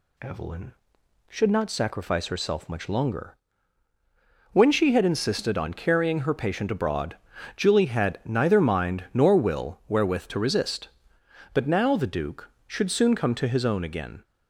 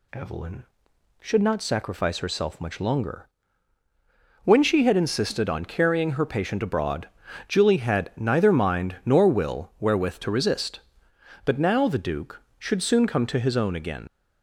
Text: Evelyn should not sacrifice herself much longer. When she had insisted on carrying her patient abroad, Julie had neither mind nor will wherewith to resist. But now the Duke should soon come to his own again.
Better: first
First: none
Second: leaves "again" unfinished; at 14.0 s; 70 ms

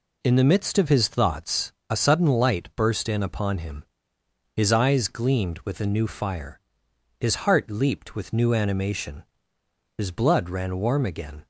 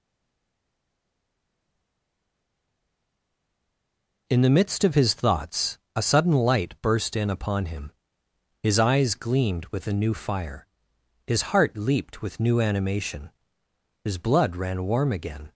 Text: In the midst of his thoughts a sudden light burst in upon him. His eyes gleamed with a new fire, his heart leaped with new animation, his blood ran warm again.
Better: first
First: pauses between "thoughts" and "a"; slight; at 1.7 s; 0.18 s long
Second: stays silent before the first word; strong; until 4.2 s; 4.2 s long // pauses between "thoughts" and "a"; slight; at 5.7 s; 0.18 s long

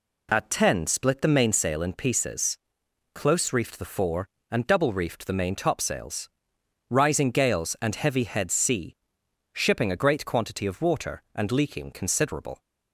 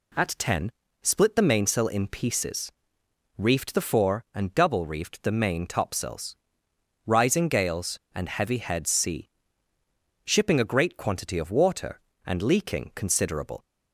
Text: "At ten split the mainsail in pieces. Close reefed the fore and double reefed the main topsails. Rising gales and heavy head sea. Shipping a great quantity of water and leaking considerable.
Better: first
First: none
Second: pauses between "ten" and "split"; slight; at 0.7 s; 0.30 s long // skips "Close"; at 3.0 s

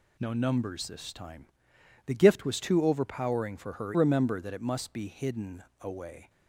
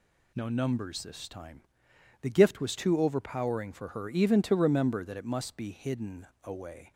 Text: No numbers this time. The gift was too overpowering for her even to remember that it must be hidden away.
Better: second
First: skips "even to"; at 3.9 s // pauses between "hidden" and "away"; slight; at 5.6 s; 0.18 s long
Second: pauses between "hidden" and "away"; slight; at 6.2 s; 0.17 s long

